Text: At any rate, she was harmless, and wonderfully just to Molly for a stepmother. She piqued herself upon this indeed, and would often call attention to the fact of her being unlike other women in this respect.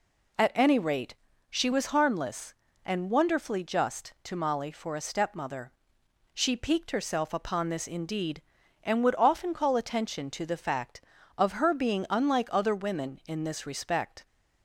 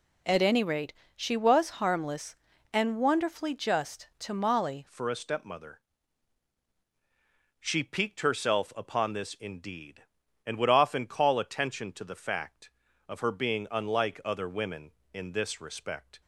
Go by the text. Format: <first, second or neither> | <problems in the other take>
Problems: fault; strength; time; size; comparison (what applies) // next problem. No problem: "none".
first | changes voice at "for"; from 4.8 s on; 11.4 s long